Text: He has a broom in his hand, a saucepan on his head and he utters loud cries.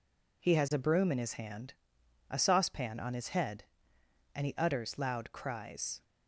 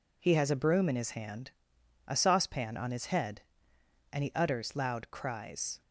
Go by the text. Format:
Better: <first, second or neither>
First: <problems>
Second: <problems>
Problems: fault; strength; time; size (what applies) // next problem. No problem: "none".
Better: neither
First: none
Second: none